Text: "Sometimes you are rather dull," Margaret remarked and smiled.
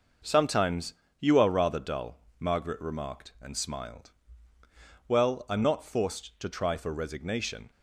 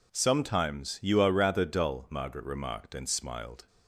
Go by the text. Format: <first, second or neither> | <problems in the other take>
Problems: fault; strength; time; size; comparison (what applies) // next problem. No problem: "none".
second | pauses between "Sometimes" and "you"; slight; at 0.9 s; 0.26 s long // goes on to say "Well I'm not forced to try for resignation"; strong; from 5.0 s on; 2.6 s long